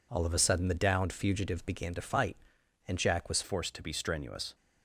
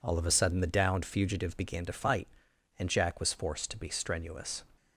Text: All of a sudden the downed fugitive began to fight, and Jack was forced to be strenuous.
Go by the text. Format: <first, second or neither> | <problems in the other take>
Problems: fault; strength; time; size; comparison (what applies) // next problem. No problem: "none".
second | changes voice at "forced"; from 3.4 s on; 1.1 s long